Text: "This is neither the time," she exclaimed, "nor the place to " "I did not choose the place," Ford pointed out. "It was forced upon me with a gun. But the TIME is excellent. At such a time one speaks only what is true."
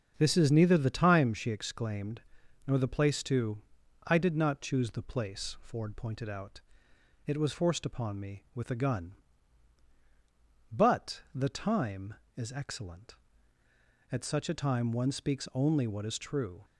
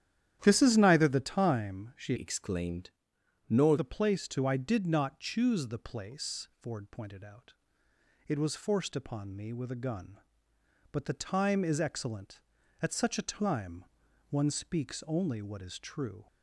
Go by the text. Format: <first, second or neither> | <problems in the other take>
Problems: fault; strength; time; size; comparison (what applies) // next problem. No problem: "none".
first | starts louder than the rest; strong; until 1.4 s; 10.5 dB; also in the first // changes voice from "exclaimed" to "nor"; from 2.1 to 3.7 s; 1.6 s long // pauses between "time" and "one"; at 13.8 s; 0.42 s long